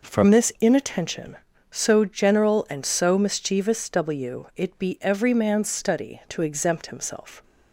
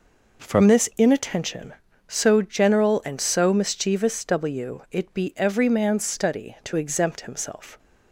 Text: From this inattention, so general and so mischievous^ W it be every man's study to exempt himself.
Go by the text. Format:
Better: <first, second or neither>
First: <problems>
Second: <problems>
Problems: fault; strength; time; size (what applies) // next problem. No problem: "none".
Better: neither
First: none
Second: none